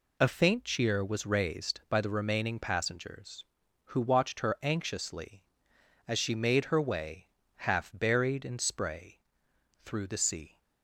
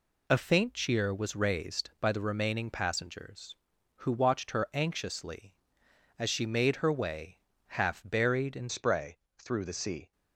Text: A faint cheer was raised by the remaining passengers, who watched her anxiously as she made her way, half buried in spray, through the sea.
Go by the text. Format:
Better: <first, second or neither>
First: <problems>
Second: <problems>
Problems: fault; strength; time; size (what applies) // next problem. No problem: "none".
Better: first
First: none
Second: changes voice at "spray"; from 8.6 s on; 1.5 s long